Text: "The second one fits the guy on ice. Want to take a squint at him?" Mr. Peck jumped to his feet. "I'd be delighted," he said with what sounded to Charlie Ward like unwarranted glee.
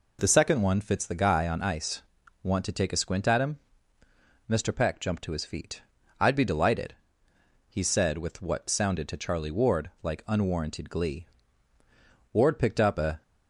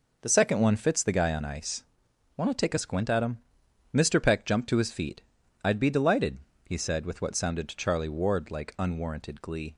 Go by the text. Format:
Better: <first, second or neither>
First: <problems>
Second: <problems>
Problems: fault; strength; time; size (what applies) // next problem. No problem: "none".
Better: second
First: goes on to say "Ward picked up a"; noticeable; from 12.3 s on; 0.88 s long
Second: none